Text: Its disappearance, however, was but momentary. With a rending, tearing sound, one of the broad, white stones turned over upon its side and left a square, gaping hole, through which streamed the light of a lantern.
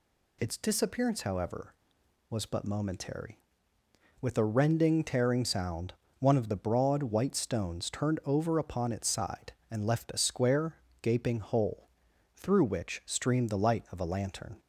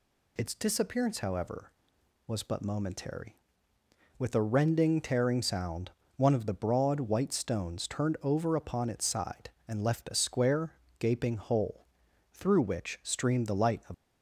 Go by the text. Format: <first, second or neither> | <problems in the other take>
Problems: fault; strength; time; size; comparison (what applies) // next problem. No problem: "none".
first | stops before "a lantern"; at 13.9 s